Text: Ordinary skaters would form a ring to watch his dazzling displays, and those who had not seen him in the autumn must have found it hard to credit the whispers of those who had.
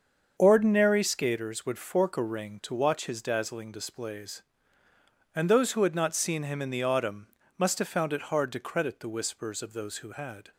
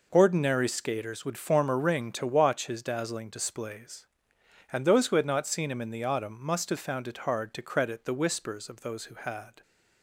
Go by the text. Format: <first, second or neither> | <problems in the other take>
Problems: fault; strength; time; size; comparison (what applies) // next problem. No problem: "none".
second | starts louder than the rest; until 1.3 s; 7 dB // says "fork" for "form"; at 1.7 s // pauses between "autumn" and "must"; slight; at 7.2 s; 0.30 s long